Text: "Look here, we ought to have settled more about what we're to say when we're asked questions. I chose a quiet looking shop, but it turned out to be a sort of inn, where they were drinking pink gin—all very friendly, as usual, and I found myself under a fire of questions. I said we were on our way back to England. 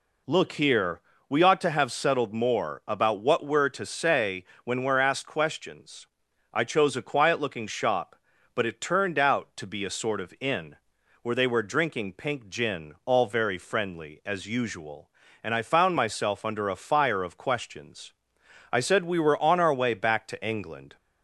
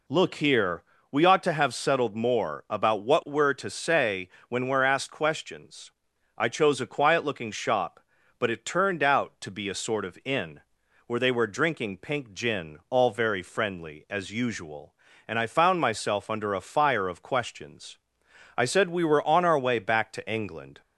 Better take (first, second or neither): neither